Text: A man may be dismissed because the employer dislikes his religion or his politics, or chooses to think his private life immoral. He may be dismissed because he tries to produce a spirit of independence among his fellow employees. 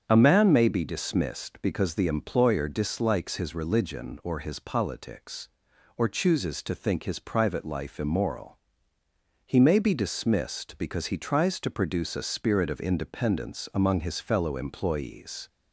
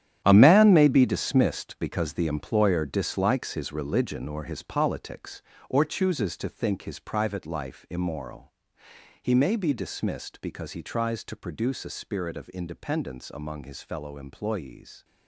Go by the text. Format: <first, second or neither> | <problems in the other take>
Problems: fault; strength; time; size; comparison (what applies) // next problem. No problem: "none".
first | gets quieter; strong; throughout; 13 dB // starts louder than the rest; strong; until 1.2 s; 11 dB; strong in the first